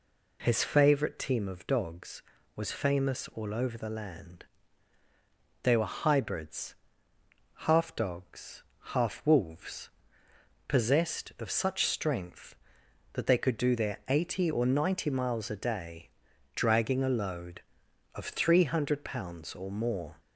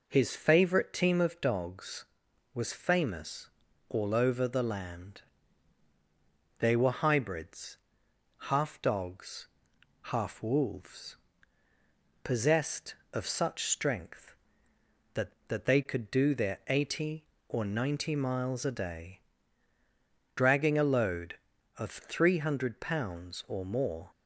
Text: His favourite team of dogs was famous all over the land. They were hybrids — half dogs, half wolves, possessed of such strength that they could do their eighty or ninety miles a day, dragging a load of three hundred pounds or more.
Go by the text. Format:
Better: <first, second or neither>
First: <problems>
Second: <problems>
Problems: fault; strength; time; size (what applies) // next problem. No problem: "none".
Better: first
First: none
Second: pauses between "famous" and "all"; at 3.4 s; 0.40 s long // says "that" twice; at 15.4 s